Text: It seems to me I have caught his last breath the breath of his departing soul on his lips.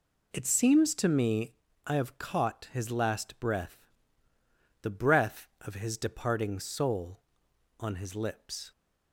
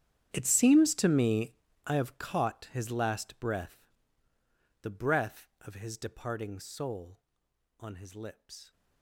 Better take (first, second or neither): first